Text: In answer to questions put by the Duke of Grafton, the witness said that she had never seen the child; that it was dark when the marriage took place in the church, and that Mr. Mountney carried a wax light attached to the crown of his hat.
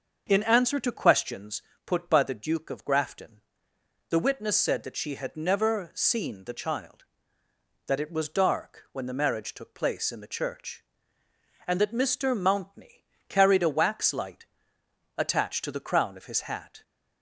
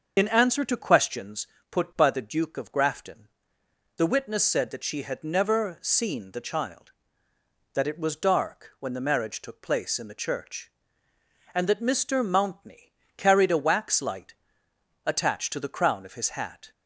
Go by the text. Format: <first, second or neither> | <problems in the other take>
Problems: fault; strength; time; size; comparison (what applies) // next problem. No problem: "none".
first | loses the start of "In"; at 0.1 s; 45 ms // starts louder than the rest; until 1.1 s; 6.5 dB; also in the first // pauses between "questions" and "put"; slight; at 1.4 s; 0.24 s long; slight in the first // pauses between "Mountney" and "carried"; slight; at 12.9 s; 0.24 s long; slight in the first // pauses between "light" and "attached"; noticeable; at 14.3 s; 0.70 s long; noticeable in the first